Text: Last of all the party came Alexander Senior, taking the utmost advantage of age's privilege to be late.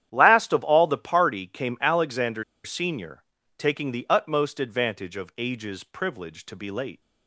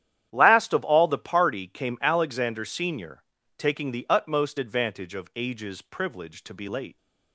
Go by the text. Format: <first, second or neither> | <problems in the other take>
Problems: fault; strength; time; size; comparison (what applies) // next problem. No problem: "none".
second | starts louder than the rest; strong; until 1.1 s; 11 dB; strong in the second // pauses between "Alexander" and "Senior"; slight; at 2.4 s; 0.22 s long